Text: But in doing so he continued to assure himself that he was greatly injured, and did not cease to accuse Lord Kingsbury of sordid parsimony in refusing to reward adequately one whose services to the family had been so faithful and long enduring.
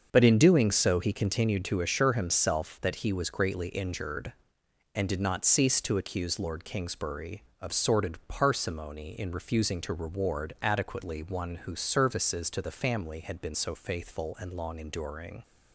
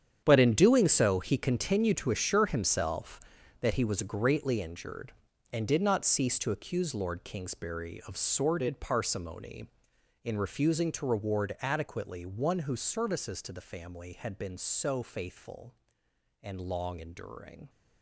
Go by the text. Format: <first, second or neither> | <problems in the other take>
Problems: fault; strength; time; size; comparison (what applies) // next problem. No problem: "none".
first | gets quieter; strong; throughout; 13.5 dB // starts louder than the rest; strong; until 1.2 s; 8.5 dB; also in the first